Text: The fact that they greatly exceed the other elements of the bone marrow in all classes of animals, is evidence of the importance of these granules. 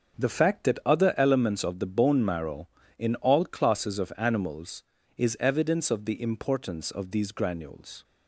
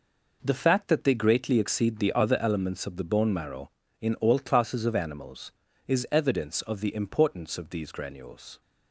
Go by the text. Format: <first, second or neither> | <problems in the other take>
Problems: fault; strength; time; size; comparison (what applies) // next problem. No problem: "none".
second | starts louder than the rest; until 1.3 s; 6.5 dB // skips "they greatly exceed the"; at 0.8 s